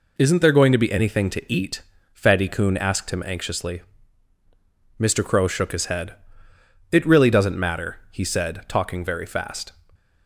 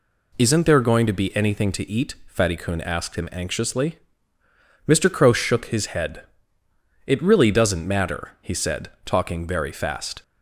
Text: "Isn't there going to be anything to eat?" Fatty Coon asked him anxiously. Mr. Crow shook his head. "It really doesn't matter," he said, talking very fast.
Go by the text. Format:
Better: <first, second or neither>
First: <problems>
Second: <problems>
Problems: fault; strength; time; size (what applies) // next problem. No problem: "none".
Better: neither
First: none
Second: none